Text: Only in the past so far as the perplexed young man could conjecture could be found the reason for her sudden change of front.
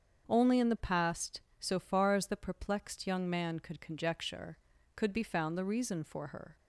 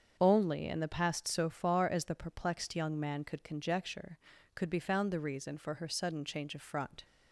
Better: second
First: starts louder than the rest; strong; until 1.3 s; 7 dB // stops before "sudden change of front"; at 6.5 s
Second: starts louder than the rest; until 1.2 s; 7 dB

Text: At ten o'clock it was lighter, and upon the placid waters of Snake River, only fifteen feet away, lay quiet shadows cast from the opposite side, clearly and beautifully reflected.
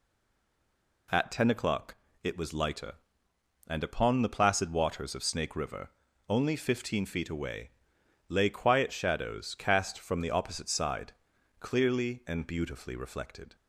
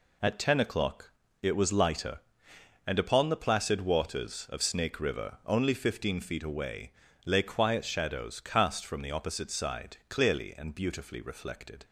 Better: second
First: stays silent before the first word; until 1.0 s; 1.0 s long // pauses between "o'clock" and "it"; slight; at 1.9 s; 0.28 s long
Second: pauses between "o'clock" and "it"; slight; at 1.1 s; 0.28 s long

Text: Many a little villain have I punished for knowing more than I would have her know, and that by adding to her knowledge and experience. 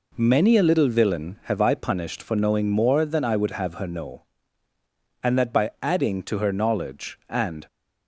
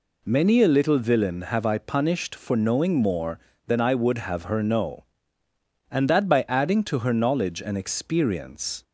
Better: second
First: stops before "experience"; at 7.6 s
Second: none

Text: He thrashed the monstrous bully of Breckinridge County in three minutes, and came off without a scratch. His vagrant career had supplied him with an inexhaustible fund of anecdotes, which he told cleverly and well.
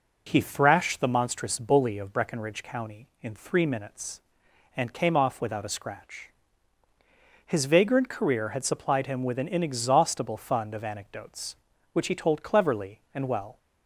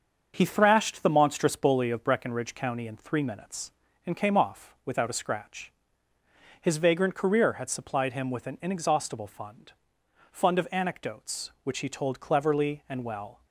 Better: first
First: none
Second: starts louder than the rest; until 1.3 s; 7 dB // says "fund" twice; at 10.3 s

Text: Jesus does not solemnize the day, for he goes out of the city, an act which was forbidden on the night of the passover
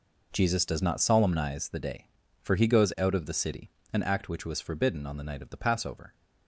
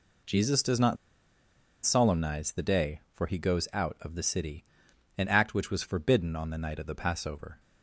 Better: first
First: none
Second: pauses between "not" and "solemnize"; noticeable; at 0.9 s; 0.89 s long

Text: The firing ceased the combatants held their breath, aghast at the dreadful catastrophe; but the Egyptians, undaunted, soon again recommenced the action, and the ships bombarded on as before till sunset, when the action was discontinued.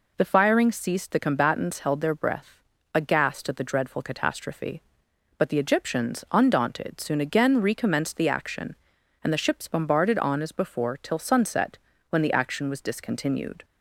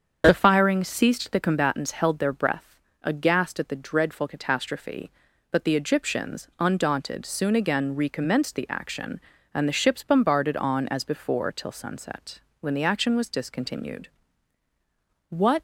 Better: first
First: none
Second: starts louder than the rest; until 1.2 s; 7 dB // goes on to say "What"; slight; from 15.2 s on; 0.32 s long

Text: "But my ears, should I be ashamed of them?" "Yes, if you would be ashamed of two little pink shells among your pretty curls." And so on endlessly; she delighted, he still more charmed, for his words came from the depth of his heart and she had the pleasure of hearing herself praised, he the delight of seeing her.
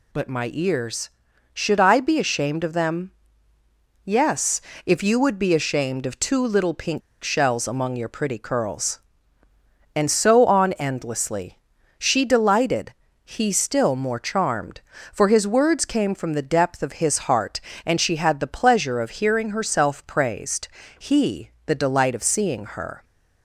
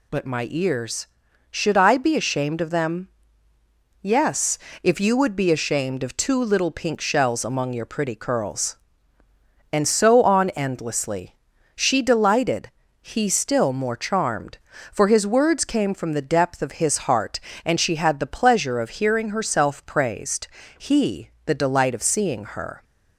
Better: second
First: pauses between "pink" and "shells"; slight; at 7.0 s; 0.22 s long // pauses between "he" and "the"; slight; at 21.4 s; 0.16 s long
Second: pauses between "he" and "the"; slight; at 21.2 s; 0.16 s long

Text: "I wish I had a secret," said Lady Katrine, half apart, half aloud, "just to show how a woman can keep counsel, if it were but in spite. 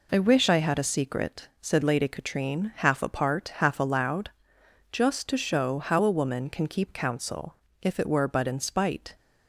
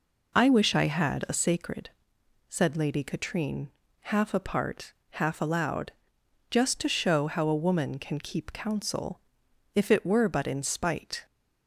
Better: first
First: none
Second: says "sacred" for "secret"; at 1.3 s

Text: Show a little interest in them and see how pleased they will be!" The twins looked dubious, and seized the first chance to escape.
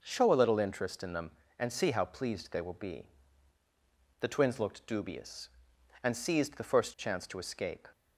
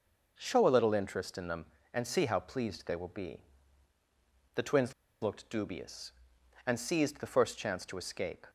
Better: first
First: none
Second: pauses between "twins" and "looked"; slight; at 4.9 s; 0.28 s long

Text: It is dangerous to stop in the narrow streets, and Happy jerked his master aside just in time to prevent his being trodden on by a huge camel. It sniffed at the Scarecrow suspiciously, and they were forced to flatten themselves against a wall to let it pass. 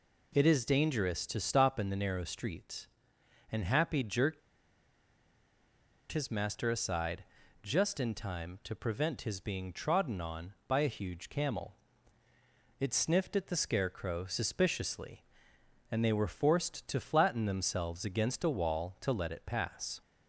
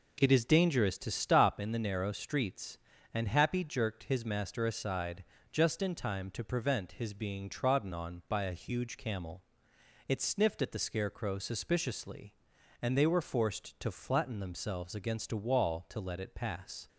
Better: second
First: pauses between "jerked" and "his"; strong; at 4.4 s; 1.7 s long // pauses between "aside" and "just"; at 7.2 s; 0.40 s long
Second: pauses between "aside" and "just"; slight; at 5.2 s; 0.30 s long

